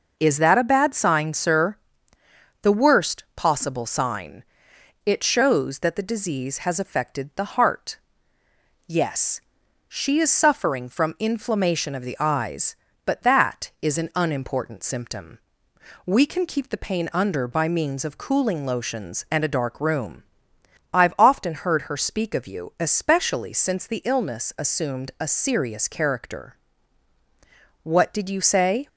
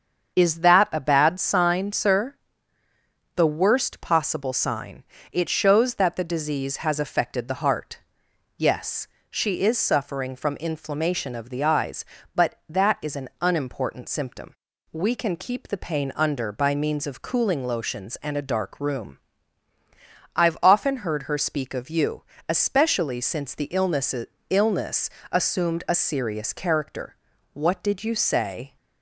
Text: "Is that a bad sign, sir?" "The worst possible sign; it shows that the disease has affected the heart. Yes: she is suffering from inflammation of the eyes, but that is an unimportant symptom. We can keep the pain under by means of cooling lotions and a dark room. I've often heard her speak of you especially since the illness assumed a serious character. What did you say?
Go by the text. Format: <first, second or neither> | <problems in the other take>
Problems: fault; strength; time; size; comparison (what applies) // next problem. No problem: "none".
first | starts louder than the rest; strong; until 1.4 s; 7 dB // pauses between "you" and "especially"; slight; at 22.2 s; 0.24 s long // says "illness" twice; at 24.4 s